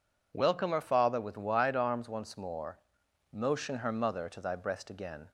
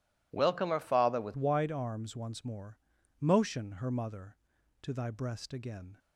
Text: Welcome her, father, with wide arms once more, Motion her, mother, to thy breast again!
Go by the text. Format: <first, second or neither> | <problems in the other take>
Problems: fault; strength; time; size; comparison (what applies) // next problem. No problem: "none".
first | changes voice at "wide"; from 1.3 s on; 4.6 s long